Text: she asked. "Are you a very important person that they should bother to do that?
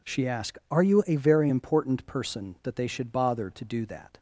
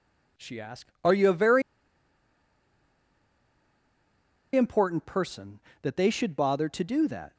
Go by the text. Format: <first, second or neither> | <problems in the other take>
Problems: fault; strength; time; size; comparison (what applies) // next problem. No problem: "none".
first | pauses between "very" and "important"; strong; at 1.6 s; 2.9 s long